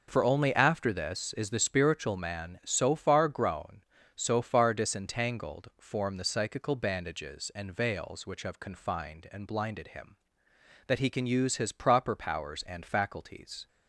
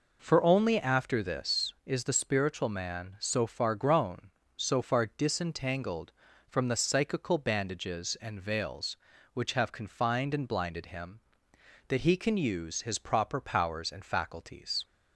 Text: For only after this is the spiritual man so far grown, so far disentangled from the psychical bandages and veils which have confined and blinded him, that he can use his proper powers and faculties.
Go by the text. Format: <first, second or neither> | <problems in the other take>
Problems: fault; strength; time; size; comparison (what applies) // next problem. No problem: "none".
second | says "form" for "from"; at 5.7 s